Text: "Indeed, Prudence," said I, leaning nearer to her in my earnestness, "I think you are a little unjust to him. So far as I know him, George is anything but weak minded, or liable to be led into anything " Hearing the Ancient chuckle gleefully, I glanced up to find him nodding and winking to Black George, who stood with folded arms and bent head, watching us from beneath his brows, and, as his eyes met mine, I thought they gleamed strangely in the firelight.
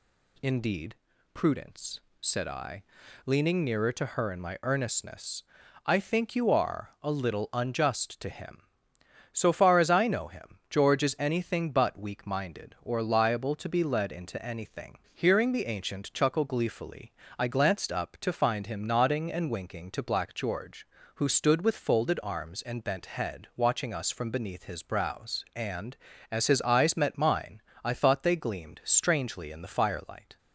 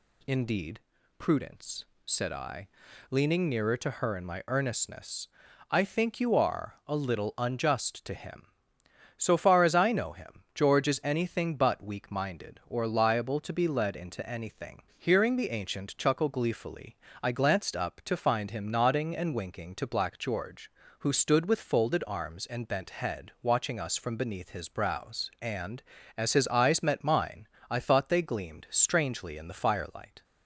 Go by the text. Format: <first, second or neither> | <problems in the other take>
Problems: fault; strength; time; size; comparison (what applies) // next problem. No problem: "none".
neither | none